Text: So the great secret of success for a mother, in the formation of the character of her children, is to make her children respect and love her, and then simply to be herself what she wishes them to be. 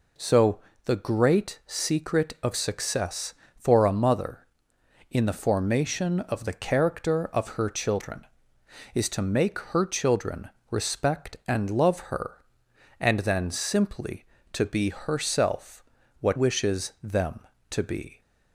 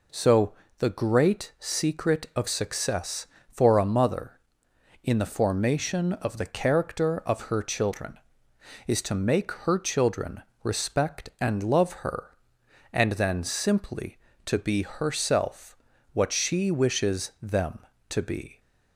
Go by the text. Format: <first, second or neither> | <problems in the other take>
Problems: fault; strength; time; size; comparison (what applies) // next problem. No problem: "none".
second | pauses between "So" and "the"; slight; at 0.5 s; 0.26 s long; slight in the second // pauses between "children" and "respect"; slight; at 10.4 s; 0.22 s long; slight in the second // pauses between "herself" and "what"; at 15.8 s; 0.38 s long; also in the second // skips "she"; at 16.3 s